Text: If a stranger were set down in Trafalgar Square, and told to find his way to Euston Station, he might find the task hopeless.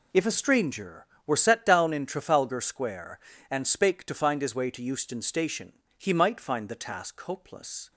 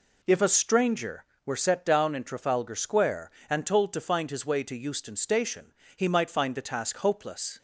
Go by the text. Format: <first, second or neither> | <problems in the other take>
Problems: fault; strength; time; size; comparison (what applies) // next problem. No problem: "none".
second | says "spake" for "told"; at 3.6 s